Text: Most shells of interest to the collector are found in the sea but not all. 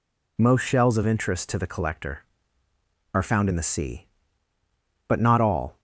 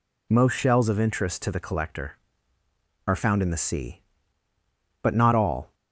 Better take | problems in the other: neither | none

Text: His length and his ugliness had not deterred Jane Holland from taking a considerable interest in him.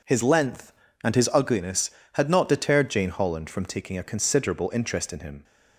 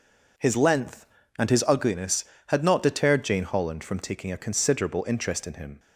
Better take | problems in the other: neither | none

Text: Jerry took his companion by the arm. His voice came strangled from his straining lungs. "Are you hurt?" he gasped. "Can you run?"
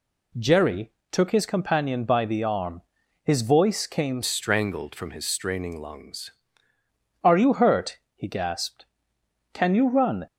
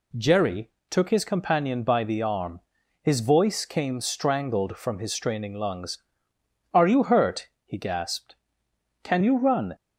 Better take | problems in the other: second | pauses between "Jerry" and "took"; slight; at 0.9 s; 0.20 s long; slight in the second // changes voice from "strangled" to "lungs"; from 4.2 to 6.3 s; 2.1 s long

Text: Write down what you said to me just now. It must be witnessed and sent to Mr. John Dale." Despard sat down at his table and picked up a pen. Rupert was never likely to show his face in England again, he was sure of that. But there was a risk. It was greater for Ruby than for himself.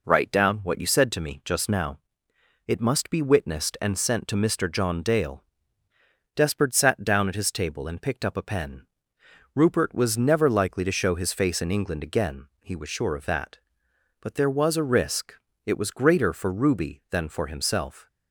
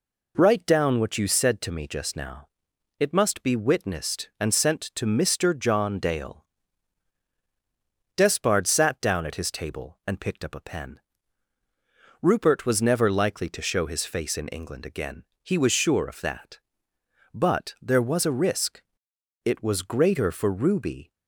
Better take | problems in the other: first | stops before "than for himself"; at 21.1 s

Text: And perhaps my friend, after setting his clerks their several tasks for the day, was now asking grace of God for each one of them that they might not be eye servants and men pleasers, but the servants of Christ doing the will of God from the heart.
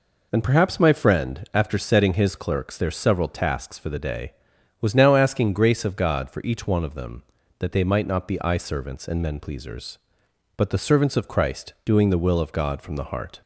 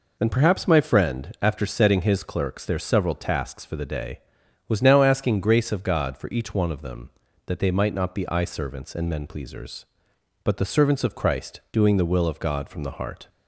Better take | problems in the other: neither | none

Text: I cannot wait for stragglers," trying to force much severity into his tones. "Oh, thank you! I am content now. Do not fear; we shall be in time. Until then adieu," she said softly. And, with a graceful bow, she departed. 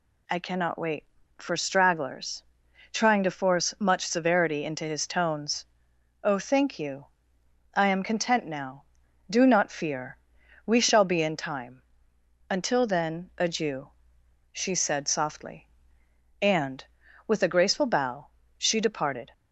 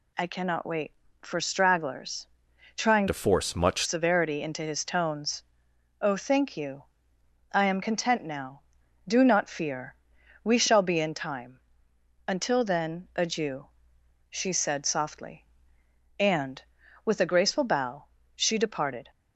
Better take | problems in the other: first | changes voice from "to" to "much"; from 3.0 to 3.8 s; 0.8 s long

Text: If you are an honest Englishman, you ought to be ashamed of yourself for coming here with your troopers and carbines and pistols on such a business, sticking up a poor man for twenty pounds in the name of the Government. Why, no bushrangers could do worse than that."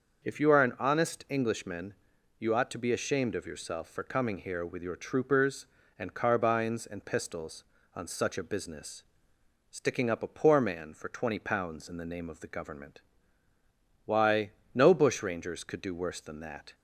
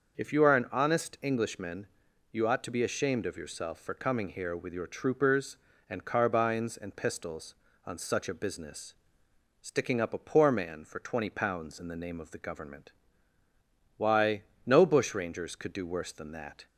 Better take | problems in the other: neither | starts louder than the rest; the same in both

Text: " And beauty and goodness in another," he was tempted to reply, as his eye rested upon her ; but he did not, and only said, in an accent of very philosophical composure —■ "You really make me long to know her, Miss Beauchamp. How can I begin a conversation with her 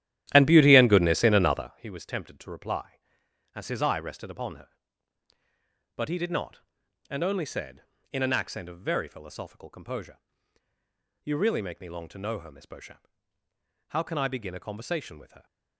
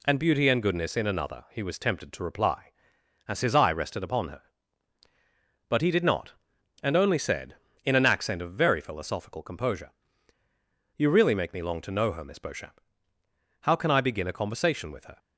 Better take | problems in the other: second | starts louder than the rest; strong; until 1.9 s; 13 dB

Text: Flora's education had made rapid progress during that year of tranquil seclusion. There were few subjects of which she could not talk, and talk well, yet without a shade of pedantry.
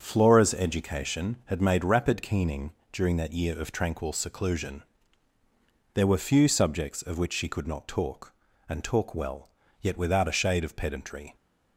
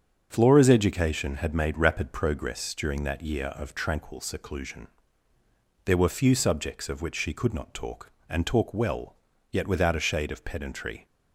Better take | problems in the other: second | starts louder than the rest; until 1.0 s; 7 dB; strong in the second // says "keening" for "progress"; at 2.2 s

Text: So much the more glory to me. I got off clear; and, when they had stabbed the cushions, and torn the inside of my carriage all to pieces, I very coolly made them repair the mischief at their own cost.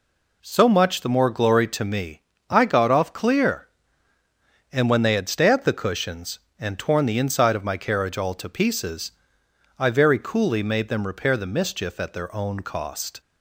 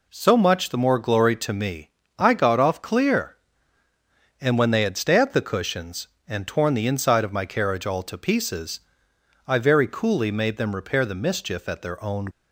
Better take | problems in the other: first | stops before "cost"; at 12.3 s

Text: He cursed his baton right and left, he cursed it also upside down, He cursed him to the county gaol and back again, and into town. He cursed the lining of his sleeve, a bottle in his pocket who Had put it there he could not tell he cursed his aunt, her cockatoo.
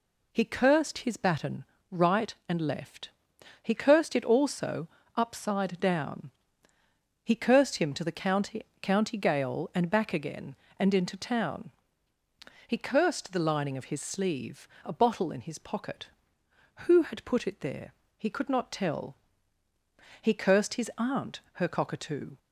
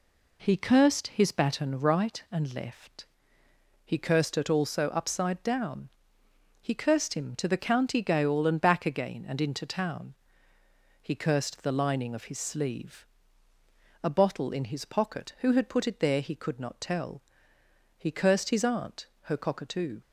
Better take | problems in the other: second | pauses between "baton" and "right"; slight; at 1.6 s; 0.26 s long // pauses between "also" and "upside"; slight; at 4.8 s; 0.26 s long // says "county" twice; at 8.7 s // pauses between "there" and "he"; slight; at 17.9 s; 0.24 s long // pauses between "tell" and "he"; at 19.1 s; 1.0 s long; noticeable in the second

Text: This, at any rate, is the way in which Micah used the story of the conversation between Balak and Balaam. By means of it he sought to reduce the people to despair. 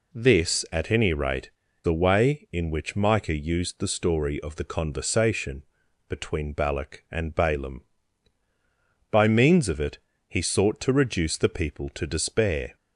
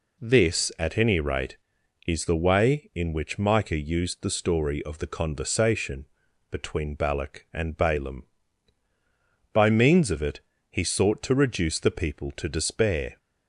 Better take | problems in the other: second | skips "is"; at 1.6 s // pauses between "conversation" and "between"; at 5.6 s; 0.44 s long; also in the second // pauses between "it" and "he"; slight; at 9.9 s; 0.32 s long; slight in the second

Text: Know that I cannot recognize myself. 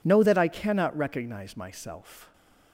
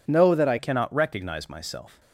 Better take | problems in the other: first | changes voice at "cannot"; from 0.5 s on; 1.4 s long

